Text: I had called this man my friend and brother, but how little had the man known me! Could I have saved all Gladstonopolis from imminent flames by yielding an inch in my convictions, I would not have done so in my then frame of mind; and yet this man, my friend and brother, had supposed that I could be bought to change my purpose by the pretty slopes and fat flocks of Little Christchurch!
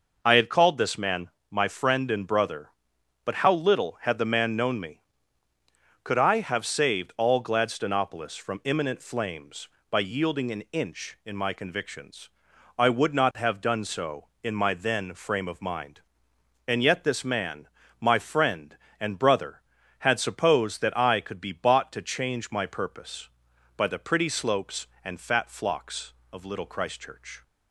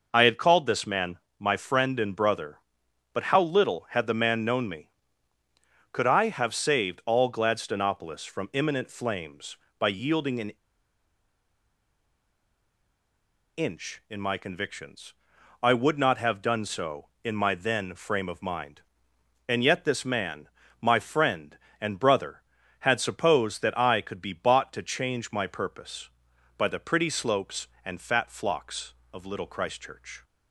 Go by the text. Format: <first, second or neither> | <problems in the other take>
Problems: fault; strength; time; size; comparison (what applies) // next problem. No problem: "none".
first | pauses between "man" and "my"; slight; at 1.1 s; 0.20 s long; slight in the first // pauses between "an" and "inch"; strong; at 10.5 s; 3.0 s long